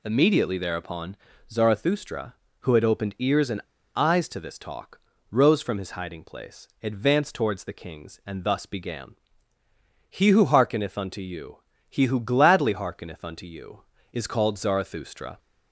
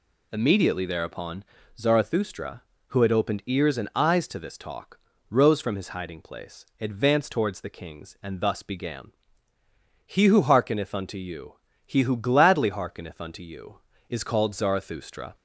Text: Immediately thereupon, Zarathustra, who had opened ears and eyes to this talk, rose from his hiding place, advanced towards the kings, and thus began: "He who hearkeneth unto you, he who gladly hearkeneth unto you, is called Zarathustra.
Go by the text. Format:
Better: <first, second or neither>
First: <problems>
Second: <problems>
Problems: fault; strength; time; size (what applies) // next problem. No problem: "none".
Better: second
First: pauses between "and" and "eyes"; slight; at 3.6 s; 0.33 s long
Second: none